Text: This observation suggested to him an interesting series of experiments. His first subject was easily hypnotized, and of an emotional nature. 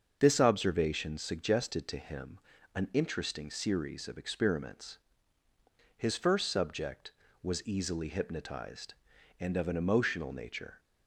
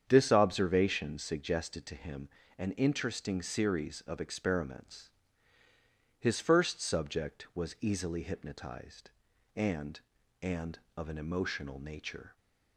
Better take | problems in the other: first | starts louder than the rest; strong; until 1.0 s; 8 dB; also in the first // pauses between "him" and "an"; slight; at 2.2 s; 0.30 s long; slight in the first // says "and" twice; at 10.4 s

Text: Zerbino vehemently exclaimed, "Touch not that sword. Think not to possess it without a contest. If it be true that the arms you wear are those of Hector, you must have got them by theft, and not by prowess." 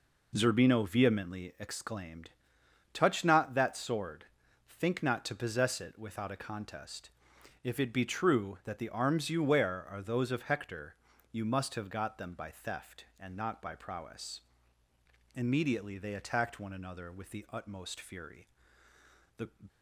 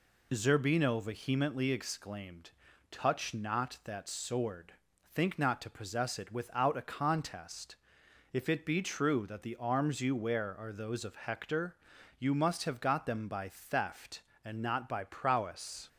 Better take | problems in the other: second | goes on to say "Immediately they attacked one another with the utmost fury The"; strong; from 15.3 s on; 4.1 s long

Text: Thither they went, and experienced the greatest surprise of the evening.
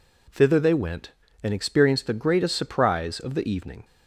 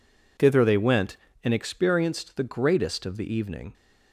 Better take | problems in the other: first | skips "surprise"; at 3.0 s

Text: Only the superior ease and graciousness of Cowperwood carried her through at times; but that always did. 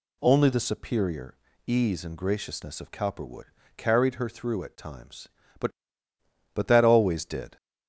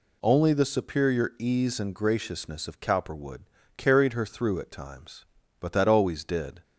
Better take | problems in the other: second | pauses between "superior" and "ease"; slight; at 1.3 s; 0.30 s long // pauses between "Cowperwood" and "carried"; slight; at 3.4 s; 0.32 s long; slight in the second // says "but" twice; at 6.5 s

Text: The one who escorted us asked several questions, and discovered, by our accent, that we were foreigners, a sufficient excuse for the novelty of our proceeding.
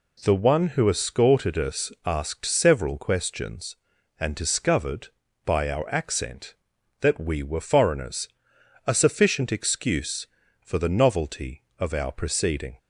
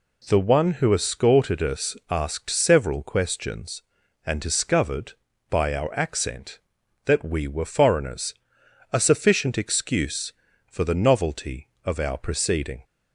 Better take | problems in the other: neither | none

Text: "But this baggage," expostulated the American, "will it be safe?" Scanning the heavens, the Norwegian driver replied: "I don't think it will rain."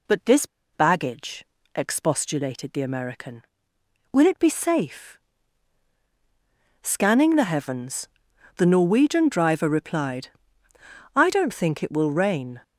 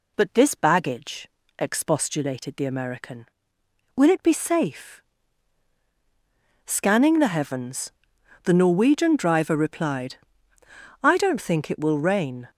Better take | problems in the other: second | pauses between "this" and "baggage"; slight; at 0.4 s; 0.27 s long

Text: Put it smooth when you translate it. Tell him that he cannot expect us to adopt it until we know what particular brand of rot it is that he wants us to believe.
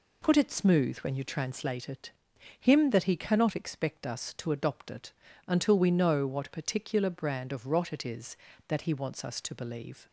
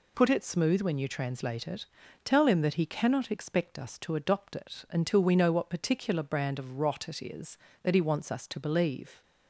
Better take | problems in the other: second | skips "Tell"; at 2.3 s // pauses between "it" and "until"; at 5.1 s; 0.38 s long

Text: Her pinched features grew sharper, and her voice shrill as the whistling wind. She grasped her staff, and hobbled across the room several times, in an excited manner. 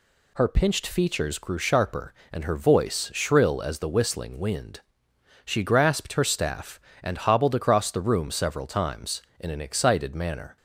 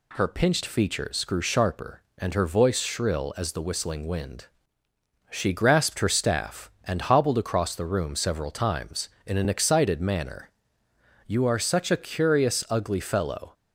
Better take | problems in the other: first | goes on to say "You are such a curious ugly fellow"; strong; from 11.2 s on; 2.2 s long

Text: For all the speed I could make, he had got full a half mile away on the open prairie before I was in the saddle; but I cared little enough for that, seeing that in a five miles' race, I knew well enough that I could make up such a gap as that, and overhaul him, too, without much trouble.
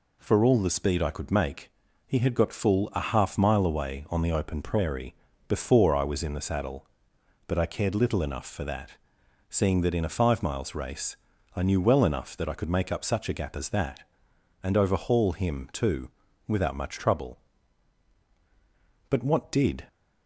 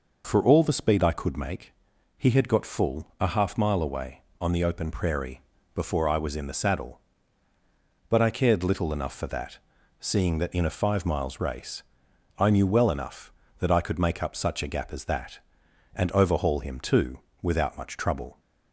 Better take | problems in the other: second | pauses between "prairie" and "before"; slight; at 5.1 s; 0.32 s long; slight in the second // goes on to say "But what did"; noticeable; from 19.0 s on; 0.80 s long

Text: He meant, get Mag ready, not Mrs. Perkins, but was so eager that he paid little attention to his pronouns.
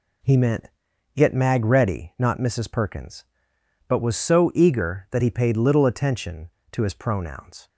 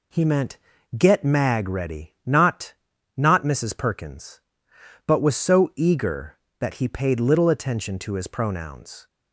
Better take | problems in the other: first | says "not" twice; at 3.1 s

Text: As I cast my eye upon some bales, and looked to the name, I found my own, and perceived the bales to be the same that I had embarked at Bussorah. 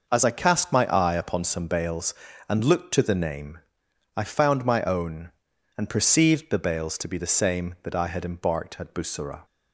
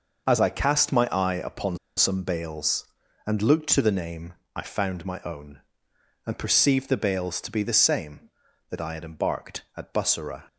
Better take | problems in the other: first | starts louder than the rest; noticeable; until 1.3 s; 6 dB // pauses between "upon" and "some"; slight; at 1.7 s; 0.20 s long

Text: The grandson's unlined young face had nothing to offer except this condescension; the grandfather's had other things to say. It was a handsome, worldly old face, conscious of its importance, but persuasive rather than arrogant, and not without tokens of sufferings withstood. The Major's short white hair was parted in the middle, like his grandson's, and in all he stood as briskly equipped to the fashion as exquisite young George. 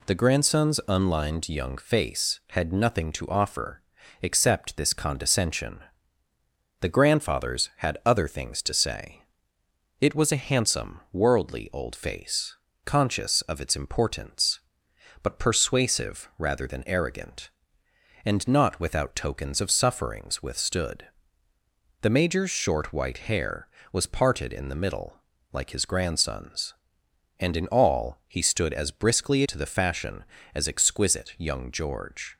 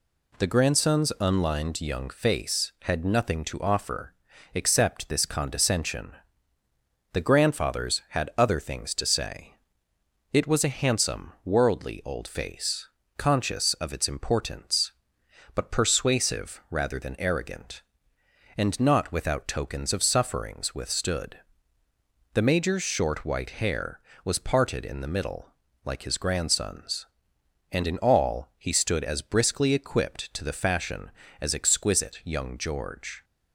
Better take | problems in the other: second | pauses between "offer" and "except"; at 3.8 s; 0.42 s long; also in the second // skips "equipped"; at 29.4 s

